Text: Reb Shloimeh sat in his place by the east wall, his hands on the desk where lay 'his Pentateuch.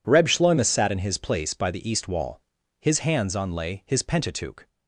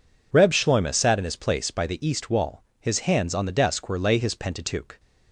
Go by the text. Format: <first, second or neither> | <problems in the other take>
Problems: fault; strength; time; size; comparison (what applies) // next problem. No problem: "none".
second | skips "the desk where"; at 3.5 s